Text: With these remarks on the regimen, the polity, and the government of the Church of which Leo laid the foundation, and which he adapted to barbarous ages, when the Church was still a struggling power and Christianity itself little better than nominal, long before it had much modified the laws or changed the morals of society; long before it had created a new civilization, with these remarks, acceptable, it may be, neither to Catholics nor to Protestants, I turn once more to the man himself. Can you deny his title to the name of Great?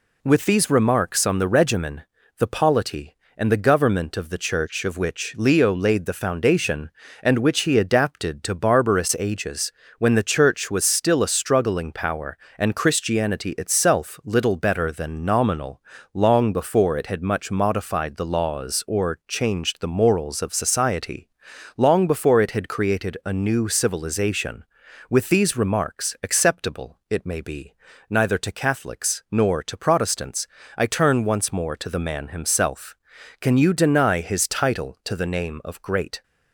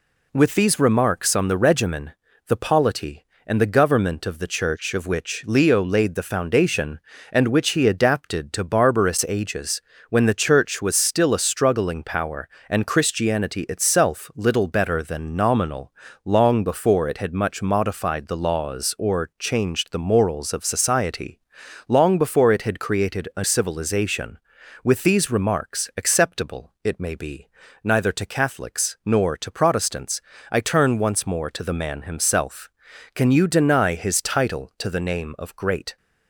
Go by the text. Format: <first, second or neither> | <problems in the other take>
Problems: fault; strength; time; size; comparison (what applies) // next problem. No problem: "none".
first | skips "new"; at 23.4 s